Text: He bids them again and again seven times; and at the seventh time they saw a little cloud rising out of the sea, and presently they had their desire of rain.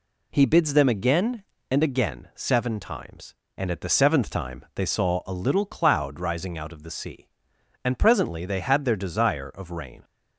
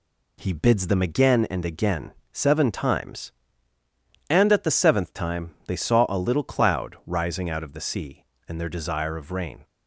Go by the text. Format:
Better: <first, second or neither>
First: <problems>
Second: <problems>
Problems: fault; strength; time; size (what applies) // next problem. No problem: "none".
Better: first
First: none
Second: pauses between "again" and "seven"; slight; at 2.1 s; 0.18 s long // pauses between "time" and "they"; slight; at 5.5 s; 0.16 s long // skips "presently they had"; at 8.5 s